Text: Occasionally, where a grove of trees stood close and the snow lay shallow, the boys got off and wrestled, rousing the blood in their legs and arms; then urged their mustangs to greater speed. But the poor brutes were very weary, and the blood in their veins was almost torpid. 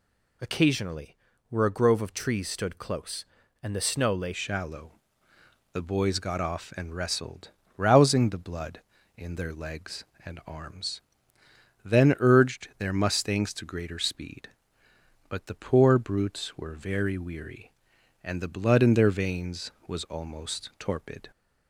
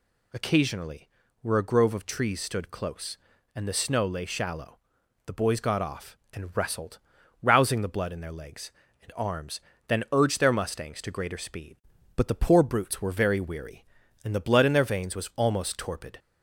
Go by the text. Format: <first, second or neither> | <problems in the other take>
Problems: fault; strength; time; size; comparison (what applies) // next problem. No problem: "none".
second | changes voice at "shallow"; from 4.3 s on; 17.0 s long